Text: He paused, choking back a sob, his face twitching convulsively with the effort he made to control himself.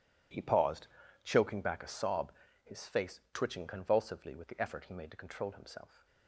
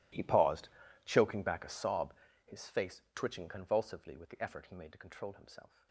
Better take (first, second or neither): first